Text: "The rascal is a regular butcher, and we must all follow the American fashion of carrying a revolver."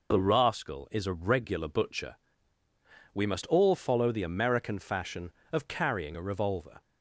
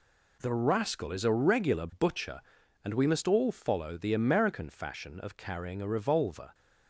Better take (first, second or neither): second